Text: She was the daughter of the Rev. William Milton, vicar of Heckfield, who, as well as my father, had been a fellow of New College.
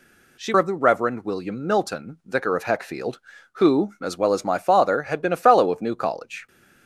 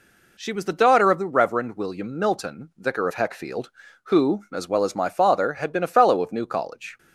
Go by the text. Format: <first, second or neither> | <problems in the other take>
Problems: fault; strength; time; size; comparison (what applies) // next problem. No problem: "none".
second | skips "was the daughter"; at 0.5 s